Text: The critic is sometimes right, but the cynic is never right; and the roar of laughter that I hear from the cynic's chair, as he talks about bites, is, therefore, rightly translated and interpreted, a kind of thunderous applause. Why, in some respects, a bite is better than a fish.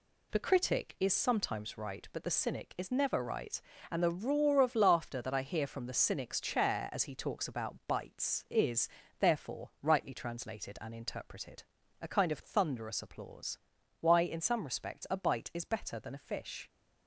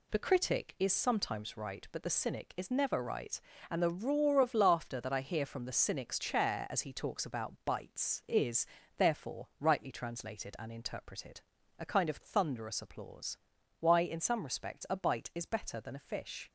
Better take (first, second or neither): neither